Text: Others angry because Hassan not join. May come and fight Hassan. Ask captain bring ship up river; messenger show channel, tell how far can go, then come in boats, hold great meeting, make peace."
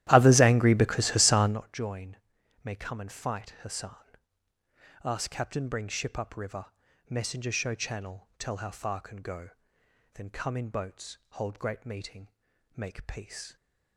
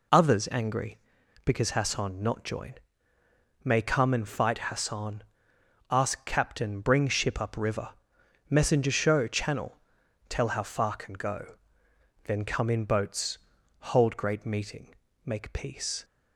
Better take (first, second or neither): second